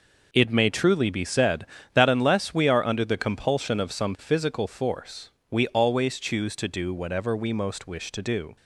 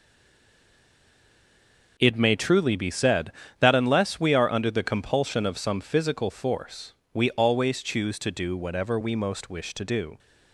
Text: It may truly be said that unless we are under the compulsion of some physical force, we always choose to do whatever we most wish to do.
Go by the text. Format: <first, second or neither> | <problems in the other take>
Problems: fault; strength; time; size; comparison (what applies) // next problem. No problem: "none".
first | stays silent before the first word; noticeable; until 1.9 s; 1.9 s long